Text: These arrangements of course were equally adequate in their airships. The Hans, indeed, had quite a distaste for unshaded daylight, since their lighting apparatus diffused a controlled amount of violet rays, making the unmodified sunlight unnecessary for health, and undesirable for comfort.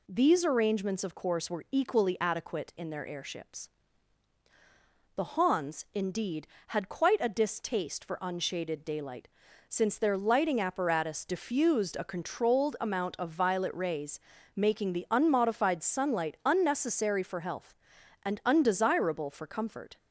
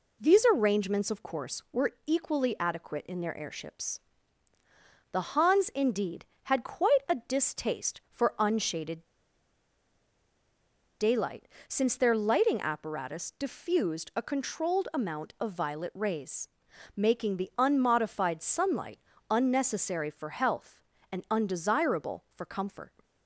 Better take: first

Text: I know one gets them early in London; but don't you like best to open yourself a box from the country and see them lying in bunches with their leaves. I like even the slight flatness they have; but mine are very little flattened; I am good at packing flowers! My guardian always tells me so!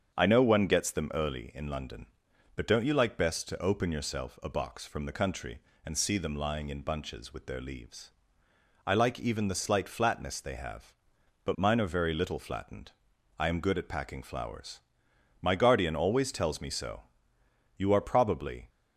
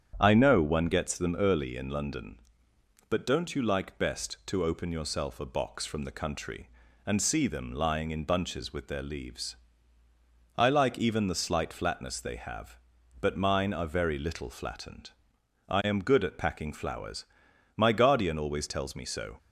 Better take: second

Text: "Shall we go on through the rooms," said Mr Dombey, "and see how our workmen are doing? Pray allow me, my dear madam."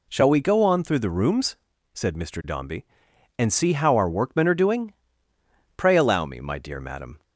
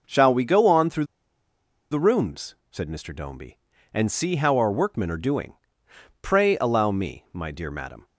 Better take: first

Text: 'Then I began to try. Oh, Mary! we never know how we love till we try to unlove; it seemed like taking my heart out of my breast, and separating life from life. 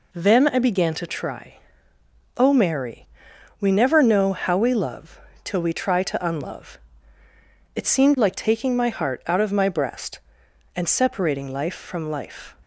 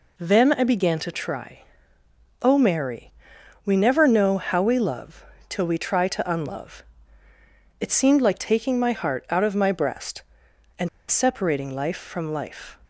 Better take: first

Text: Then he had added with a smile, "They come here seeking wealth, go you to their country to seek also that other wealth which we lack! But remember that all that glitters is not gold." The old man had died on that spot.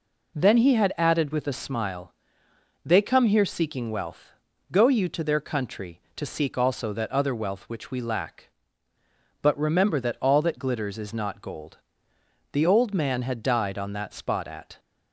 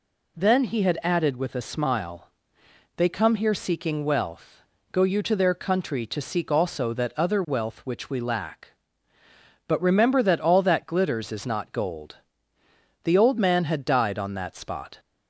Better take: second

